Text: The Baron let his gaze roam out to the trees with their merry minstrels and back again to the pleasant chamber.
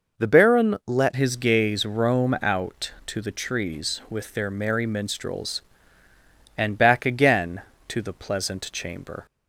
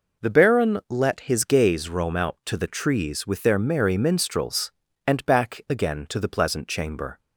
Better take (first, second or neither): second